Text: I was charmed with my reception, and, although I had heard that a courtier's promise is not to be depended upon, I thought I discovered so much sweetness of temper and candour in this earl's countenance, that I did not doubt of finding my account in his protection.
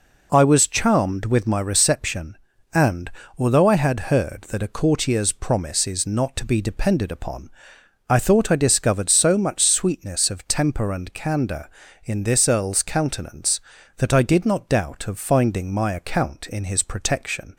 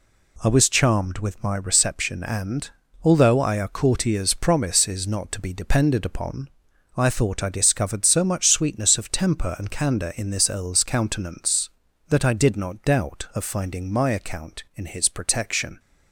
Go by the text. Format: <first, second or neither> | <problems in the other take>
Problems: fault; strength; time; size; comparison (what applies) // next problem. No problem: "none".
first | skips "had heard that"; at 3.5 s